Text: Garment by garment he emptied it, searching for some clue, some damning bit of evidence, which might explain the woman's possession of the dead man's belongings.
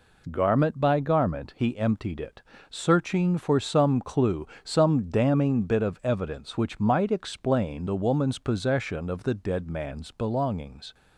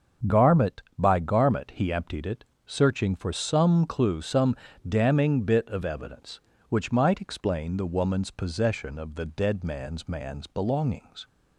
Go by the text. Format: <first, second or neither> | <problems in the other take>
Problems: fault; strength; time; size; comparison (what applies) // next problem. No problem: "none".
first | starts louder than the rest; strong; until 1.4 s; 7 dB // pauses between "some" and "damning"; slight; at 4.5 s; 0.32 s long // says "man's" twice; at 10.0 s